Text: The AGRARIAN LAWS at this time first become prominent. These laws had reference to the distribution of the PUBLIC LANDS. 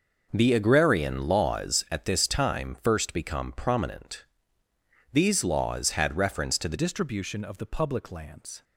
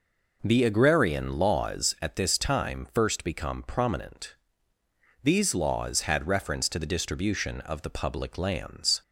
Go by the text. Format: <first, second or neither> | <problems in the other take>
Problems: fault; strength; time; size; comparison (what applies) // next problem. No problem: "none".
second | changes voice at "distribution"; from 6.7 s on; 1.9 s long